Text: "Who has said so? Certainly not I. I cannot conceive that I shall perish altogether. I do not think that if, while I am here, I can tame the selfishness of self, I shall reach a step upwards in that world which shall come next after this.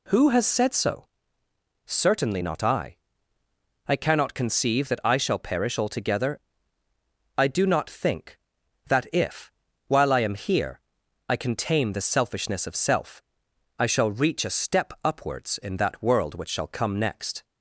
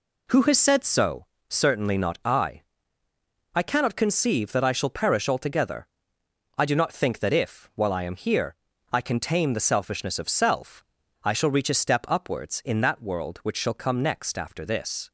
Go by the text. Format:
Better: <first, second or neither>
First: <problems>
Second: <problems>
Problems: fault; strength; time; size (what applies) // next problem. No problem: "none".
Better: second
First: stops before "after this"; at 17.4 s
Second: none